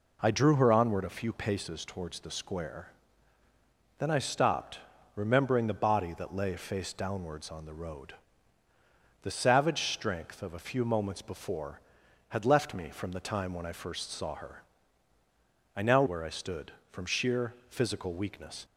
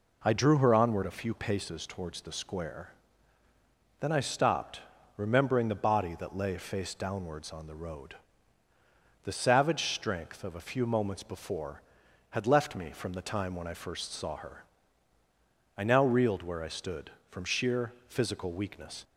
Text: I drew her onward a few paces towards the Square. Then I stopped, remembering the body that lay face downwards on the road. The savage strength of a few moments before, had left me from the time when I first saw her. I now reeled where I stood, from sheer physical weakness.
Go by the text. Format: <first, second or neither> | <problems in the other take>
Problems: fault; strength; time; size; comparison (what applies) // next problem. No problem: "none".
second | skips "reeled"; at 16.0 s // pauses between "sheer" and "physical"; slight; at 17.5 s; 0.16 s long; slight in the second